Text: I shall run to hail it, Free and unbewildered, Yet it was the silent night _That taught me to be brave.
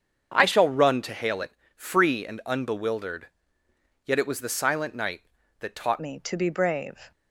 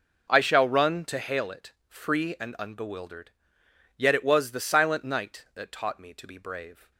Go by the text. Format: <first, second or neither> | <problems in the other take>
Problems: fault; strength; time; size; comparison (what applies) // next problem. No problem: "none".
second | starts louder than the rest; strong; until 1.3 s; 7 dB // changes voice at "me"; from 5.9 s on; 1.2 s long